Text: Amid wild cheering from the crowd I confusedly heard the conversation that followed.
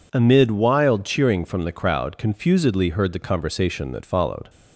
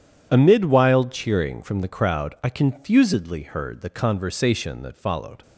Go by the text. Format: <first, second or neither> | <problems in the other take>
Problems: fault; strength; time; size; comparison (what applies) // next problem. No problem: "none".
second | skips "I"; at 2.1 s